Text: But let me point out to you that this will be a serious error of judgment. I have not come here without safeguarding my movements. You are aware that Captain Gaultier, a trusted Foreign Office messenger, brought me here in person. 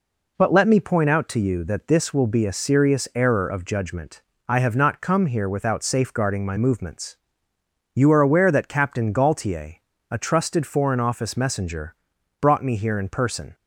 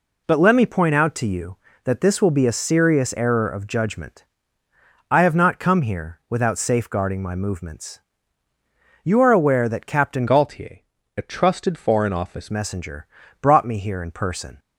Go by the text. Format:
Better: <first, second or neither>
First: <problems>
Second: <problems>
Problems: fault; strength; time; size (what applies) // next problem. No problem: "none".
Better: first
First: none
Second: changes voice from "Gaultier" to "Office"; from 10.2 to 12.5 s; 2.3 s long